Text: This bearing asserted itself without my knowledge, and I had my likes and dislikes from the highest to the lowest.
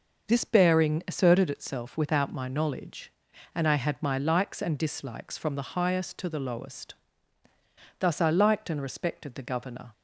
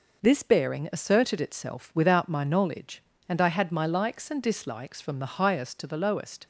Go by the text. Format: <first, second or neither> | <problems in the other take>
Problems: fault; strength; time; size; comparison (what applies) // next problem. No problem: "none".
second | goes on to say "Thus I liked and respected the Governor"; strong; from 8.0 s on; 1.9 s long